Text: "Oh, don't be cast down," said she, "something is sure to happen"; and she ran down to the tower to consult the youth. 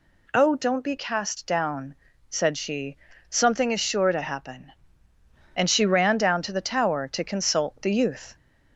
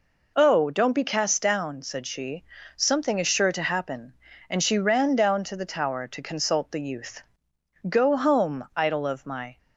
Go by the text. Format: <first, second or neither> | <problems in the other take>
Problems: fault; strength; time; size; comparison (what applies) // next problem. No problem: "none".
first | goes on to say "Go home idol of my"; strong; from 7.8 s on; 1.6 s long